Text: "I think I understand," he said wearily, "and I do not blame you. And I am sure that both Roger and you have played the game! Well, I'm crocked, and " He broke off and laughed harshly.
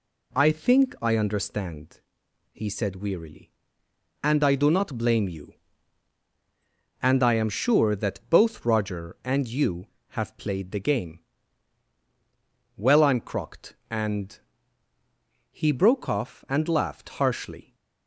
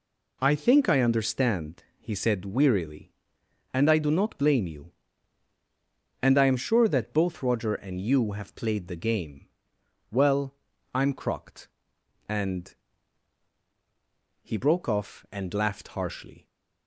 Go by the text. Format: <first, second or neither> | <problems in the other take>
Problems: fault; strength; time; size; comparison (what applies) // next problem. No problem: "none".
neither | none